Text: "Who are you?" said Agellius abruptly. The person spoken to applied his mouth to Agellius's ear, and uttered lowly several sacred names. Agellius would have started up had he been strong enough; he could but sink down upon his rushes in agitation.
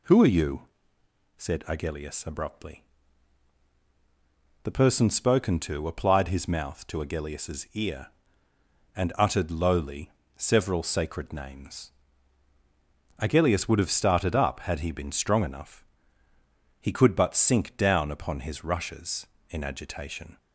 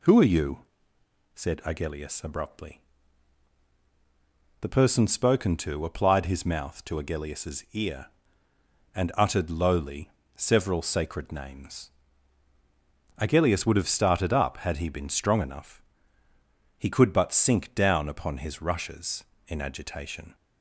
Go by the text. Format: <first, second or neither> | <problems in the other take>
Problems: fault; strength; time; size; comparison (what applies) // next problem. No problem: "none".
neither | pauses between "lowly" and "several"; slight; the same in both